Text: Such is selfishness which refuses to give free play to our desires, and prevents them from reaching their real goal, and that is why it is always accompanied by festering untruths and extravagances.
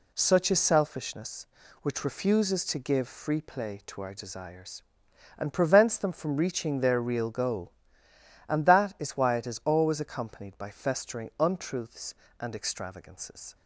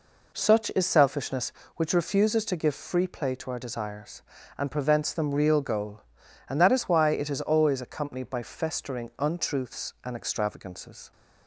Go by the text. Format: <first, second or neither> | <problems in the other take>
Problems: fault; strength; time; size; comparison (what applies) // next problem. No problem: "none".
first | skips "from reaching their"; at 5.3 s